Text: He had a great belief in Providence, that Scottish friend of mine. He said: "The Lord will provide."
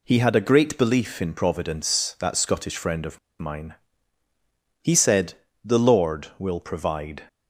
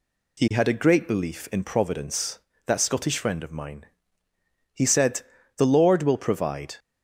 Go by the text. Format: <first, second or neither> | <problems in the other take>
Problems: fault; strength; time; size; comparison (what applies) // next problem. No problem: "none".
second | pauses between "of" and "mine"; slight; at 3.1 s; 0.22 s long